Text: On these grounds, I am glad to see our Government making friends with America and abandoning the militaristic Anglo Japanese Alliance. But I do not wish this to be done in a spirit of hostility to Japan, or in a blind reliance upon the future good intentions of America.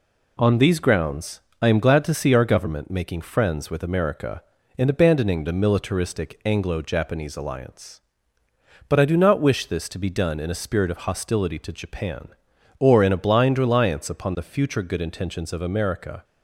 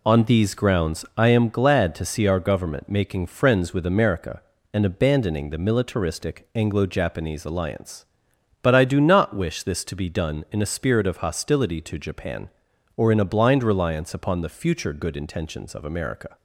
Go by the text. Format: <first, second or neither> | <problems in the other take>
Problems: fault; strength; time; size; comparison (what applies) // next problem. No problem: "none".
neither | none